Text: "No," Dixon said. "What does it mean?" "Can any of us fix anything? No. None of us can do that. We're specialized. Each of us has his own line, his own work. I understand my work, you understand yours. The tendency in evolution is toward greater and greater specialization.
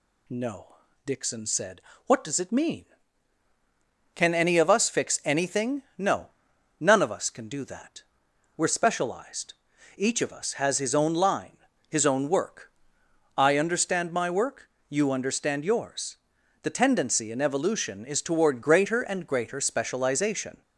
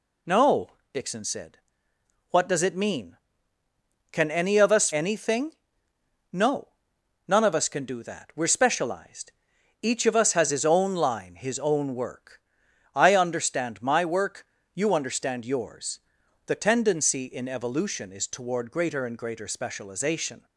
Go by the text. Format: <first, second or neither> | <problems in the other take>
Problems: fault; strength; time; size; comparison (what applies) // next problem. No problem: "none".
first | skips "fix"; at 4.9 s